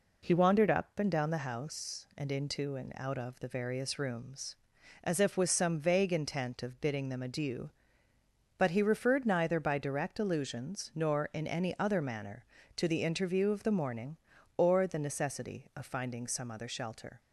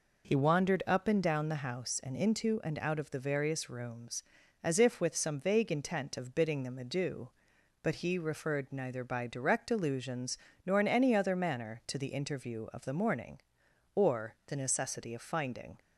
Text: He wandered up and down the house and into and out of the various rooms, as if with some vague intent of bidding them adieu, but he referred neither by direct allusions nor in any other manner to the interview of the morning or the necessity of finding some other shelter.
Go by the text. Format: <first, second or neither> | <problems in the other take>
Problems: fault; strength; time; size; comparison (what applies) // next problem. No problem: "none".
first | pauses between "allusions" and "nor"; slight; at 10.3 s; 0.30 s long // stops before "some other shelter"; at 15.7 s